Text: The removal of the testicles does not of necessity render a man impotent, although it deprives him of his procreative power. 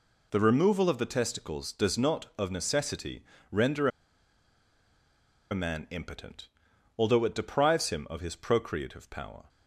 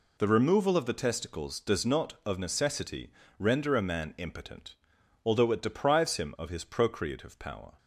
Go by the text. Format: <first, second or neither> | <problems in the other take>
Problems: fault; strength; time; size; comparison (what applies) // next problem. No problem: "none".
second | pauses between "necessity" and "render"; slight; at 3.2 s; 0.26 s long; slight in the second // pauses between "render" and "a"; strong; at 3.8 s; 1.6 s long